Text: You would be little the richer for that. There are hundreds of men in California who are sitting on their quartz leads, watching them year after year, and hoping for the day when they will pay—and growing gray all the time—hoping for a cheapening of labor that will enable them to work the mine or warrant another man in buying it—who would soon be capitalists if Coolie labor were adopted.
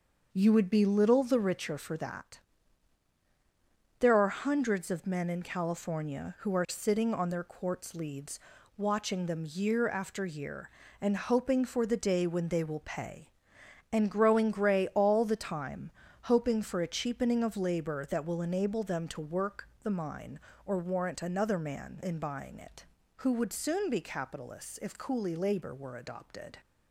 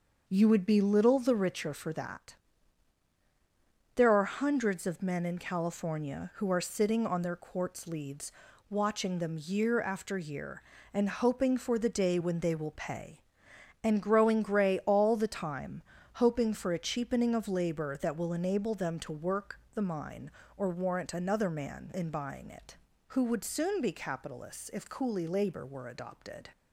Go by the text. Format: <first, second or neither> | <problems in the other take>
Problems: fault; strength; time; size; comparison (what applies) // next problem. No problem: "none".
neither | starts louder than the rest; the same in both // pauses between "work" and "the"; slight; the same in both